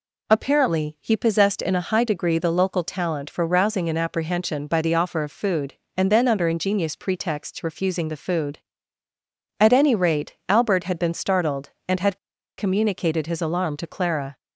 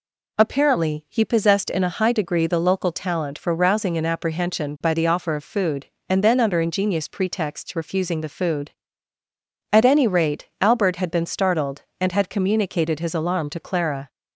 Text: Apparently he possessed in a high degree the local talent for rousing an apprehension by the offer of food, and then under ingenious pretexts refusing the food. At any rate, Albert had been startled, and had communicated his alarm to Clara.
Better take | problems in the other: second | pauses between "had" and "communicated"; at 12.1 s; 0.40 s long

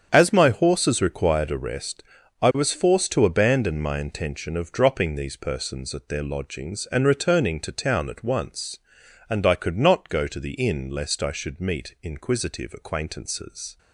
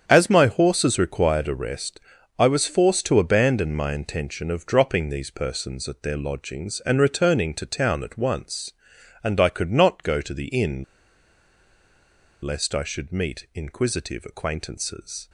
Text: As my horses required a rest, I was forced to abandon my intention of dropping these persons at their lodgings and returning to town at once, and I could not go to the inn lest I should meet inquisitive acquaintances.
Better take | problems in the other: first | starts louder than the rest; strong; until 1.0 s; 8 dB; strong in the first // pauses between "inn" and "lest"; strong; at 10.8 s; 1.5 s long

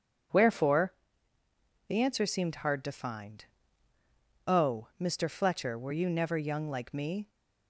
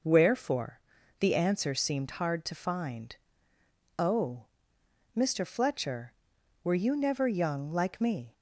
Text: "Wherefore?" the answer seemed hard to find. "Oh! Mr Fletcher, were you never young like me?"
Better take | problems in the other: neither | none

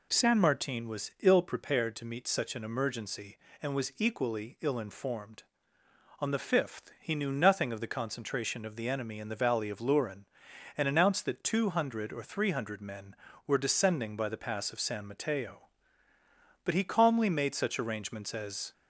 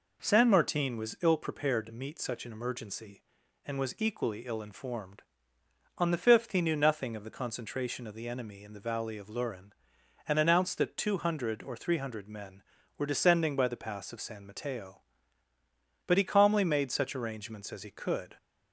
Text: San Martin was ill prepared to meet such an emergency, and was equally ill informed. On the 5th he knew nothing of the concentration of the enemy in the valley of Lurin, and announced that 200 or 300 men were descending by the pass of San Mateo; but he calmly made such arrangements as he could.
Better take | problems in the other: second | stops before "he could"; at 18.7 s

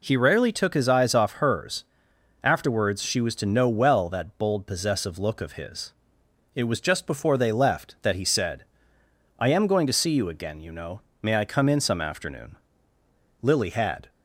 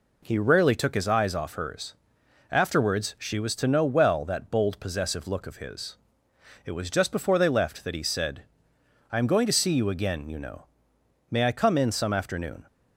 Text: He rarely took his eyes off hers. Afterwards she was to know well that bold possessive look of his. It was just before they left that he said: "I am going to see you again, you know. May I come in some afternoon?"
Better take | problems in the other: second | goes on to say "Lily had"; noticeable; from 13.4 s on; 0.68 s long

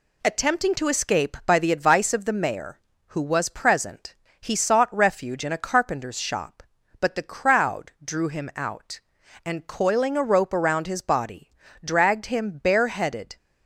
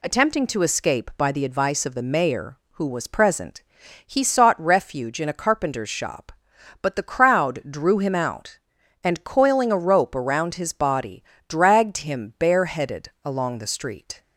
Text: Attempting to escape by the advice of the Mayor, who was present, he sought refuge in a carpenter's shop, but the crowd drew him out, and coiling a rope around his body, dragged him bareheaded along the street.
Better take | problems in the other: second | stops before "along the street"; at 13.3 s

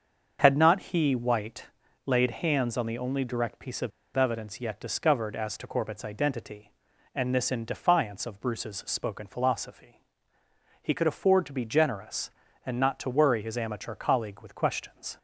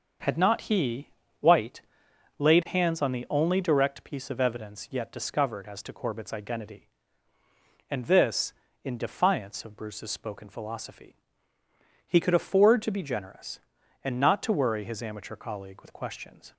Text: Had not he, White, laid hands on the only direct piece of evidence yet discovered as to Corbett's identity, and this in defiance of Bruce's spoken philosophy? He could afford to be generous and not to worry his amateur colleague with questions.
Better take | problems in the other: second | starts louder than the rest; until 1.4 s; 6.5 dB // pauses between "of" and "evidence"; slight; at 3.9 s; 0.25 s long

